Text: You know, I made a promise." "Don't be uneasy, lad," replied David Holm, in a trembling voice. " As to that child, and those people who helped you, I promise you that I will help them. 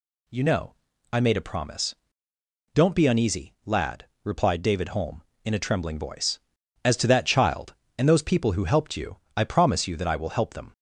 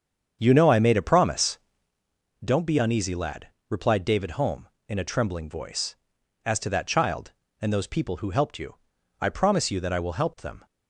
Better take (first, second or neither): first